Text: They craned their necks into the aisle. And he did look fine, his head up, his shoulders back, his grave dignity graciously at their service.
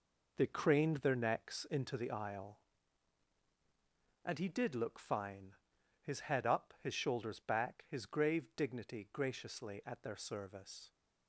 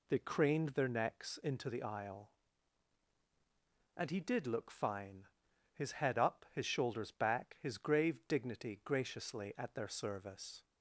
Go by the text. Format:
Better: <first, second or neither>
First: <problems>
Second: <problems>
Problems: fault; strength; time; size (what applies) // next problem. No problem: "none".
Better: second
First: gets quieter; strong; throughout; 8.5 dB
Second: none